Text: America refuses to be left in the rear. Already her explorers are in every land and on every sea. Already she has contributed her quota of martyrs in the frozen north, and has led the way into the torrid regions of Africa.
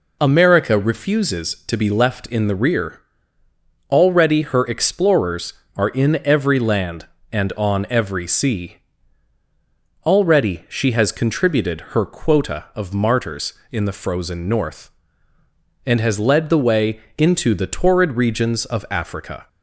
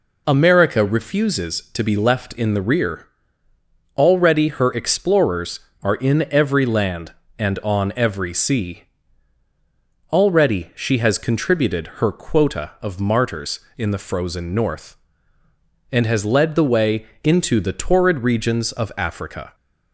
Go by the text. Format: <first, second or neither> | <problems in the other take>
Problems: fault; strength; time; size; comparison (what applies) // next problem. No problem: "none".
neither | pauses between "way" and "into"; slight; the same in both